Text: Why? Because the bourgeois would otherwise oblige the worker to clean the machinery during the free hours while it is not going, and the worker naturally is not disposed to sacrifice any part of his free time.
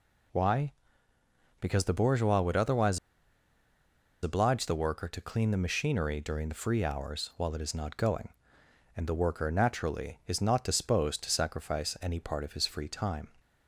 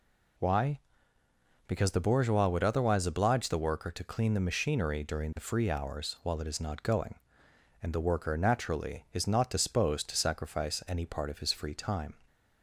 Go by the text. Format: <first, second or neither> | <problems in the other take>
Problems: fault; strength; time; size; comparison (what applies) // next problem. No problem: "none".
second | pauses between "otherwise" and "oblige"; strong; at 2.9 s; 1.2 s long